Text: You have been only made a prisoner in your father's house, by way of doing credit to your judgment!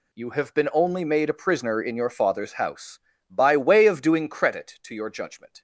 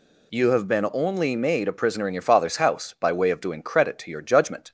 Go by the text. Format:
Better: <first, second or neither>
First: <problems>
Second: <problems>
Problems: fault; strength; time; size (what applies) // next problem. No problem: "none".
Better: neither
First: none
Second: none